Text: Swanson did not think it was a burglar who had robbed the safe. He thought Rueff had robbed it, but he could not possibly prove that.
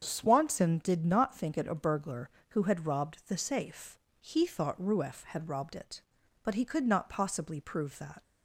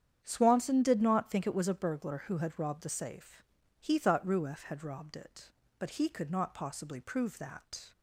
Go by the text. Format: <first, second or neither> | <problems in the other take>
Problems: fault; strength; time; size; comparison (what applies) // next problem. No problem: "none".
second | starts louder than the rest; strong; until 1.0 s; 7.5 dB; strong in the second // skips "was"; at 1.6 s